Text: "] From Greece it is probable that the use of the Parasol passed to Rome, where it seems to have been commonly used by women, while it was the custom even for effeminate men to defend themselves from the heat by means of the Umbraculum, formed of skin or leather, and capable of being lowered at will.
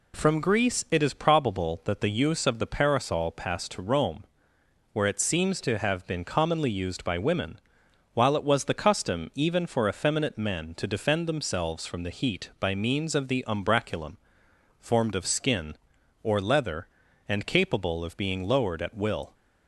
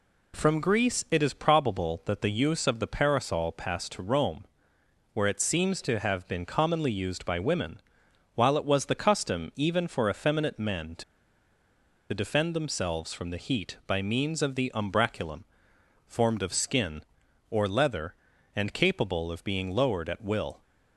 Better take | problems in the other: first | pauses between "to" and "defend"; at 11.0 s; 1.0 s long

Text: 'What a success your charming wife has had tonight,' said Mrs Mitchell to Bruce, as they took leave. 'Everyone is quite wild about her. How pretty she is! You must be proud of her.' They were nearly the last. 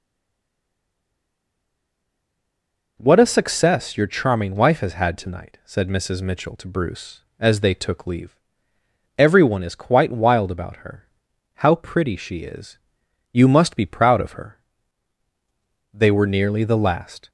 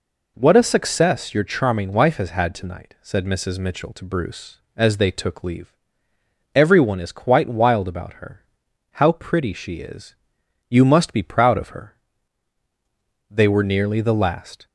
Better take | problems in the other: second | stays silent before the first word; strong; until 2.9 s; 2.9 s long

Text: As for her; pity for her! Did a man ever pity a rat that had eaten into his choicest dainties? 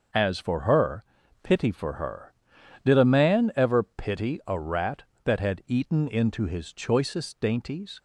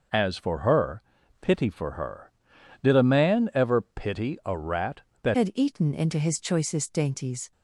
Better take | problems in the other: first | changes voice at "had"; from 5.3 s on; 2.2 s long

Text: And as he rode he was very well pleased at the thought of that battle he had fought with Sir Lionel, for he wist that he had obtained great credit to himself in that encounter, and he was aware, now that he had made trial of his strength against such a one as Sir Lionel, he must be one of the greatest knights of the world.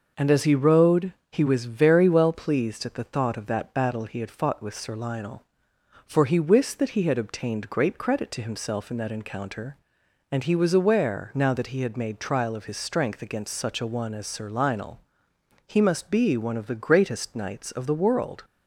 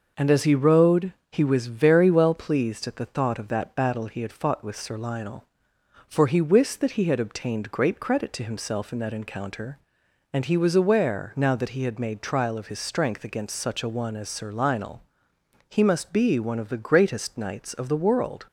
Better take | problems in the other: neither | pauses between "rode" and "he"; slight; the same in both

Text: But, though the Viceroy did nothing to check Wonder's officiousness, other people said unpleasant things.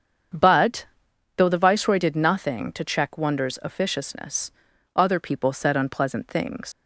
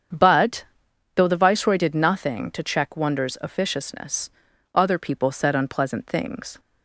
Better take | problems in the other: second | starts louder than the rest; strong; until 1.8 s; 7.5 dB; strong in the second // leaves "things" unfinished; at 6.7 s; 85 ms

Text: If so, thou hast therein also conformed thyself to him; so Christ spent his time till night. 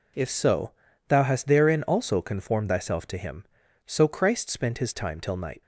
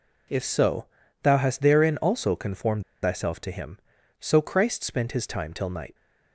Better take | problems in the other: first | pauses between "conformed" and "thyself"; slight; at 2.8 s; 0.19 s long

